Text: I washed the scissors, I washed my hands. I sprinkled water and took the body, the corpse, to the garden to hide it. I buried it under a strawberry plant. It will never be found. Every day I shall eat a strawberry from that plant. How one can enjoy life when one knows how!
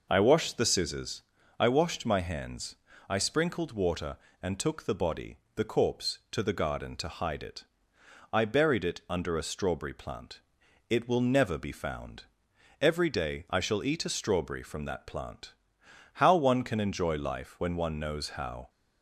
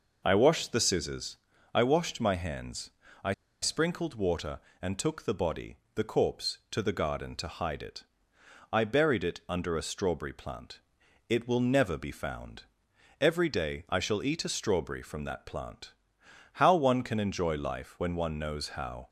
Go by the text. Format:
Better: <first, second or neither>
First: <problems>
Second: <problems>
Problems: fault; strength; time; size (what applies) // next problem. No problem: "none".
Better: first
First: none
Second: pauses between "I" and "sprinkled"; slight; at 3.3 s; 0.29 s long